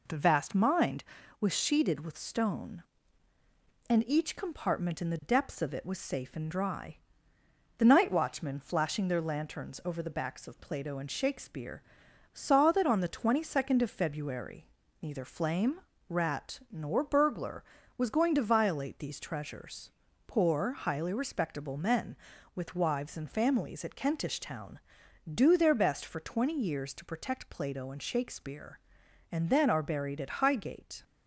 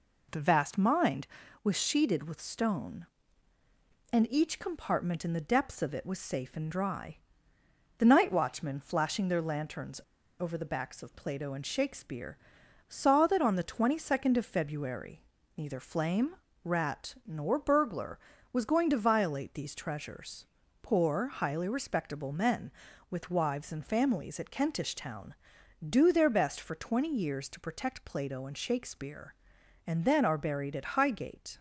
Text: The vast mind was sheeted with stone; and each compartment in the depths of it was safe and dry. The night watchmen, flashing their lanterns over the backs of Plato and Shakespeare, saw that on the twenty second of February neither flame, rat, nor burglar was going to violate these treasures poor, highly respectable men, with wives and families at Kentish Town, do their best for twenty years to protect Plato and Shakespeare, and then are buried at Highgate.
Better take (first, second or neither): first